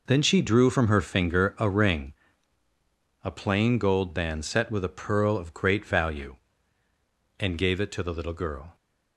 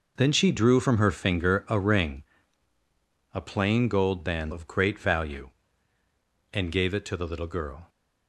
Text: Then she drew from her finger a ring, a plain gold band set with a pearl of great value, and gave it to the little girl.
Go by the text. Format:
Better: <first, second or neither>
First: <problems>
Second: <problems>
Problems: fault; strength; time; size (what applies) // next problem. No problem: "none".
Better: first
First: none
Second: skips "set with a pearl"; at 4.5 s